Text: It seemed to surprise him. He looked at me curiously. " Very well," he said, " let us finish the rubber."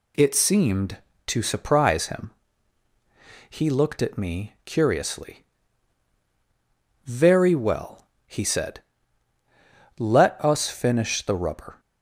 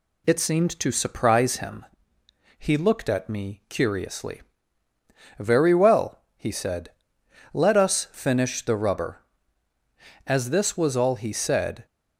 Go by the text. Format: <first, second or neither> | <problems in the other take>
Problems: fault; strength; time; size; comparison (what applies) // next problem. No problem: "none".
first | goes on to say "As this was all he said"; from 10.2 s on; 1.6 s long